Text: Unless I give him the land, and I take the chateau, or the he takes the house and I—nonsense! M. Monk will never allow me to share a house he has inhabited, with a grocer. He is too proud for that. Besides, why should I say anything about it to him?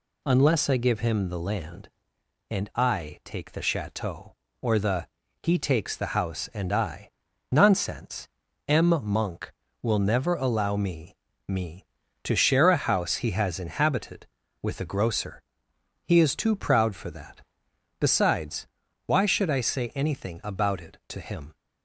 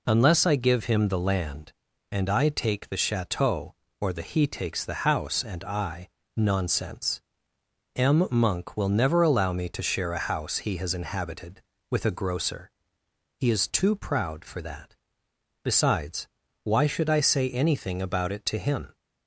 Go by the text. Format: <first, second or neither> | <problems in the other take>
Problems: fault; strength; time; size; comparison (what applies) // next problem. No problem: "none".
second | pauses between "the" and "he"; slight; at 5.0 s; 0.34 s long // says "me" twice; at 11.4 s